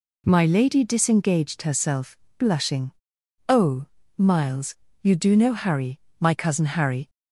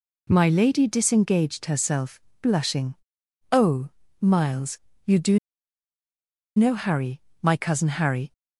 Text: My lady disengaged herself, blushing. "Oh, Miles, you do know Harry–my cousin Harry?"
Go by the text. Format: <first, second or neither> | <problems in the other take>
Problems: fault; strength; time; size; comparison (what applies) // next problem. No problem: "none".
first | pauses between "do" and "know"; at 5.3 s; 1.1 s long